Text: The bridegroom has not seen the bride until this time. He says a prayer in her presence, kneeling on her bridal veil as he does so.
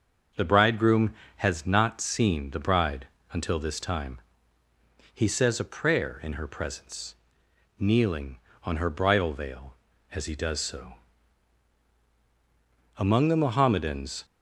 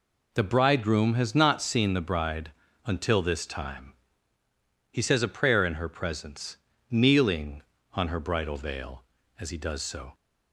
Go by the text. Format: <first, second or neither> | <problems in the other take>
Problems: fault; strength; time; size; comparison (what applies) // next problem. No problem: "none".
second | starts louder than the rest; until 1.5 s; 6.5 dB // pauses between "bride" and "until"; slight; at 3.0 s; 0.28 s long; slight in the second // goes on to say "Among the Mohammedans"; noticeable; from 12.9 s on; 1.2 s long